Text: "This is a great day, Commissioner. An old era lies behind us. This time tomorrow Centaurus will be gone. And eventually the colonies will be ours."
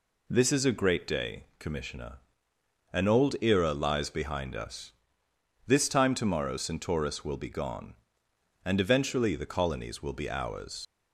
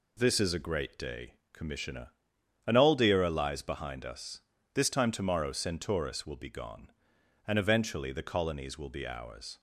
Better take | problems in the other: second | leaves "ours" unfinished; at 10.8 s; 60 ms

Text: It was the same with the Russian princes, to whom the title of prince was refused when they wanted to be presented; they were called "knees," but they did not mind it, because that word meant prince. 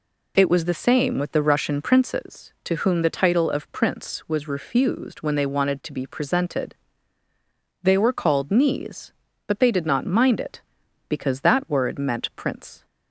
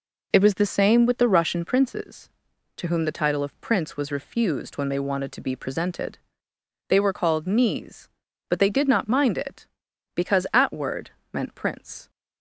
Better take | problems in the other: first | says "at" for "that"; at 10.5 s // pauses between "word" and "meant"; slight; at 11.0 s; 0.22 s long

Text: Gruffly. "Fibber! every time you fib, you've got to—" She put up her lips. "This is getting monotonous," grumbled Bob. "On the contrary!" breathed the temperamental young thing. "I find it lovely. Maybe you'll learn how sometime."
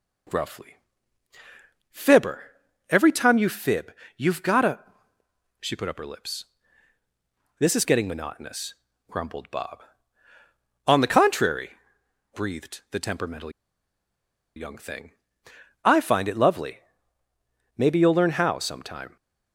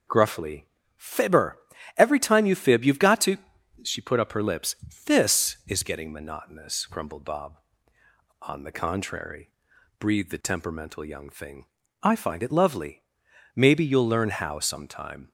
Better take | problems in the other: second | pauses between "temperamental" and "young"; at 13.4 s; 1.0 s long

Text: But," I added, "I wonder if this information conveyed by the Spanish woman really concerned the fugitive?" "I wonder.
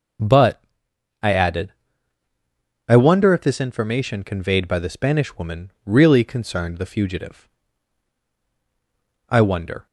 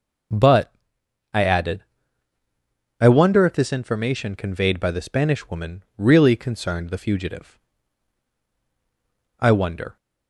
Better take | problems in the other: neither | none

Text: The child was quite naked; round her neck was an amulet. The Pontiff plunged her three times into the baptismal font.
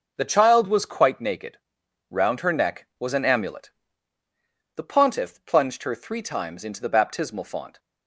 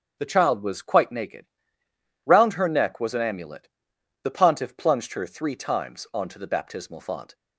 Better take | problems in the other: first | starts louder than the rest; strong; until 1.2 s; 7.5 dB // says "onto" for "into"; at 6.1 s

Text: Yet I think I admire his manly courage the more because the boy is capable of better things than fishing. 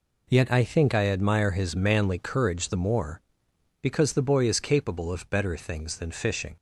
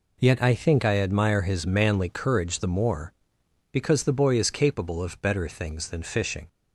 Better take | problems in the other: neither | none

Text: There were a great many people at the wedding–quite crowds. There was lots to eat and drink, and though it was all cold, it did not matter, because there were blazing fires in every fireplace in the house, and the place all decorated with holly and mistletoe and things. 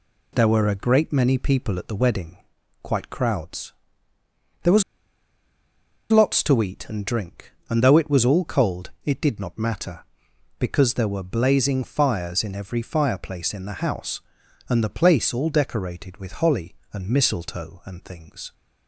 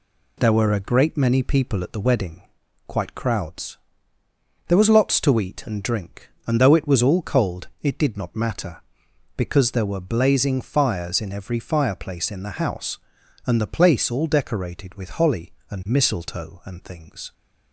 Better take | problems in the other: second | pauses between "was" and "lots"; strong; at 4.8 s; 1.2 s long

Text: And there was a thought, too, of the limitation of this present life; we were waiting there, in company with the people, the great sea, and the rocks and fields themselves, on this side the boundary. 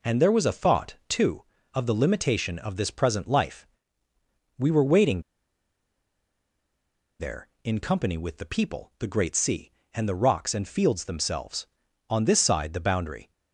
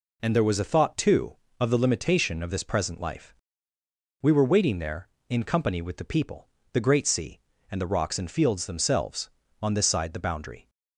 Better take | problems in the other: second | pauses between "waiting" and "there"; strong; at 5.2 s; 1.9 s long

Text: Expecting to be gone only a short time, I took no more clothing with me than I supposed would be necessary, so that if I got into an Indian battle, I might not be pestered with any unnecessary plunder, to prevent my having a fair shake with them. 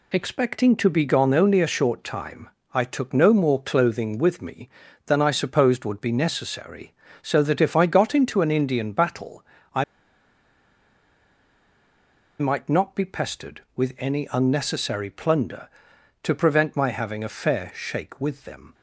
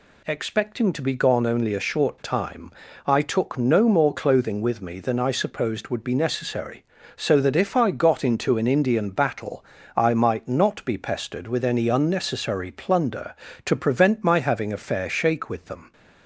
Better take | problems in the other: second | pauses between "I" and "might"; strong; at 9.8 s; 2.5 s long

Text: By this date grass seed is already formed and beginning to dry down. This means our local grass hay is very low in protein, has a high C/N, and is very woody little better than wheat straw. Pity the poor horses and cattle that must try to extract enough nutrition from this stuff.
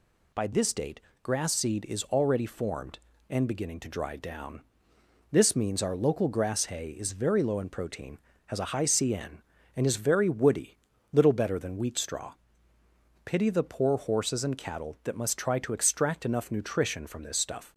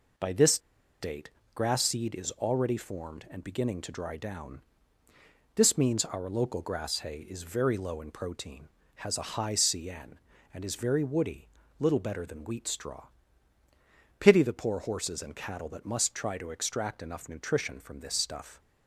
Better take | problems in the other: first | pauses between "this" and "date"; at 0.5 s; 0.43 s long // pauses between "date" and "grass"; slight; at 1.2 s; 0.24 s long; slight in the first // pauses between "woody" and "little"; slight; at 11.4 s; 0.32 s long; slight in the first

